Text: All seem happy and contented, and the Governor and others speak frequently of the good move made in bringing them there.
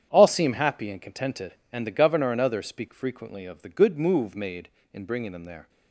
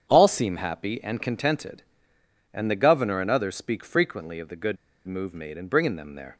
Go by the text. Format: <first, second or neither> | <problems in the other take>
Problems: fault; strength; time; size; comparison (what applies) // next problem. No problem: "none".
first | starts louder than the rest; strong; until 1.0 s; 8 dB; strong in the first // pauses between "good" and "move"; slight; at 4.7 s; 0.31 s long